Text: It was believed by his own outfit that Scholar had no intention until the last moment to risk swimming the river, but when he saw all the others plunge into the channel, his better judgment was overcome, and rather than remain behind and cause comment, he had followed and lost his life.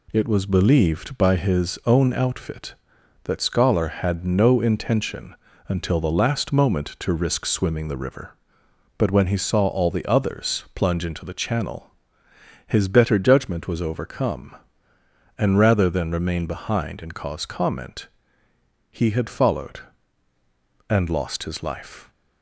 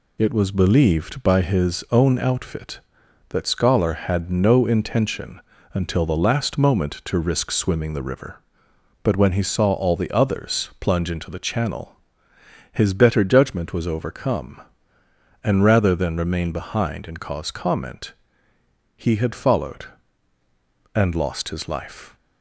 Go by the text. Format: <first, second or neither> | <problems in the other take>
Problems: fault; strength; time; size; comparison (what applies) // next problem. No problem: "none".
first | loses the start of "It"; at 0.1 s; 40 ms // pauses between "intention" and "until"; slight; at 5.4 s; 0.32 s long; slight in the first